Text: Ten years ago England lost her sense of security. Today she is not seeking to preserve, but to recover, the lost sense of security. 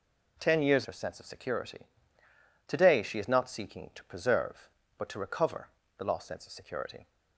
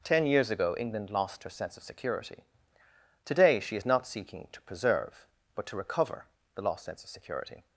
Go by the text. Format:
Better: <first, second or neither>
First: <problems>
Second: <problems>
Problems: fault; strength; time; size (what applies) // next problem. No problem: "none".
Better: second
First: skips "ago England lost"; at 0.8 s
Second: none